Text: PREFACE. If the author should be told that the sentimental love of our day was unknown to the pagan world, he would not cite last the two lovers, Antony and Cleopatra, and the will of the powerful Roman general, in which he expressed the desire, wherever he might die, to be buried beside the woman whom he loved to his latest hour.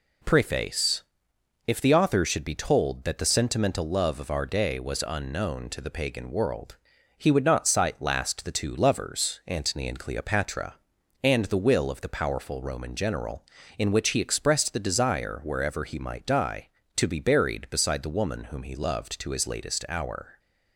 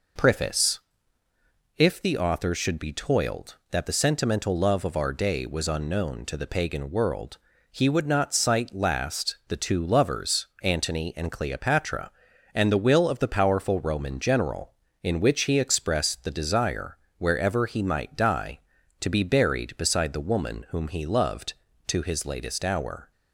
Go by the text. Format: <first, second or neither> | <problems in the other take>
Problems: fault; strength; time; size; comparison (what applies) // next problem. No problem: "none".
first | says "toiled" for "told"; at 2.9 s